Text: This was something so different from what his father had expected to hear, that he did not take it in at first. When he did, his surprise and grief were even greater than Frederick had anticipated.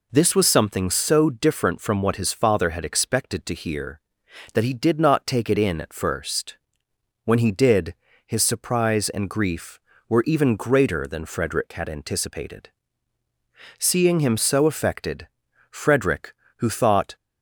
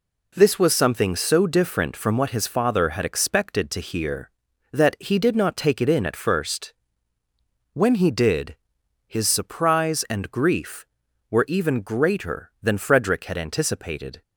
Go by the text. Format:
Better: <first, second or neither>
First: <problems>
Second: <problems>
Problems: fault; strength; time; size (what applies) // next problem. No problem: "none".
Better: second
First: goes on to say "Seeing him so affected Frederick who thought"; strong; from 13.7 s on; 3.3 s long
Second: none